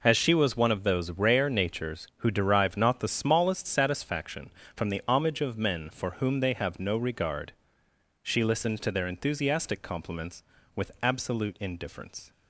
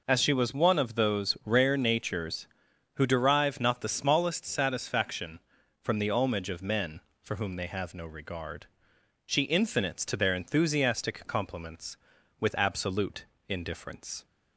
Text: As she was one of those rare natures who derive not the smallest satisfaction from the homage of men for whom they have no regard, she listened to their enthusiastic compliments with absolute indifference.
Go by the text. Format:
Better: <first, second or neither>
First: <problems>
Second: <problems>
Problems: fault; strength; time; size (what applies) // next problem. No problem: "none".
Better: first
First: none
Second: says "infinites" for "listened"; at 9.4 s // pauses between "absolute" and "indifference"; slight; at 13.2 s; 0.22 s long